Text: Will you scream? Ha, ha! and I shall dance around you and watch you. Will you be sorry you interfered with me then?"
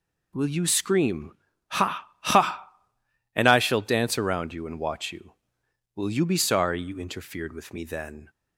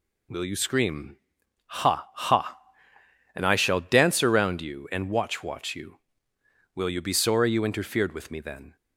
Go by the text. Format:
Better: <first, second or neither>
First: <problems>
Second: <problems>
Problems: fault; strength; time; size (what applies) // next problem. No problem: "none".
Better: first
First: none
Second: says "watch" twice; at 5.4 s